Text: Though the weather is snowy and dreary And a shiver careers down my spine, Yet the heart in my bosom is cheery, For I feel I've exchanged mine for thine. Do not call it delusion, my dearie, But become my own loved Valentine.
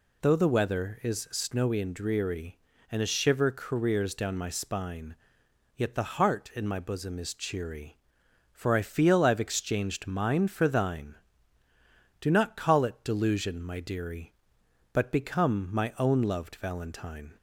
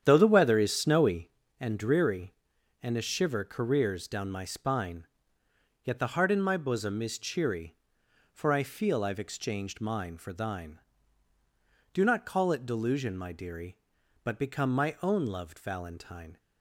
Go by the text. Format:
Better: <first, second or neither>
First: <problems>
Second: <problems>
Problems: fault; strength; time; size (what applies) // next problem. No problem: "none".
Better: first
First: none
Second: starts louder than the rest; strong; until 1.3 s; 9 dB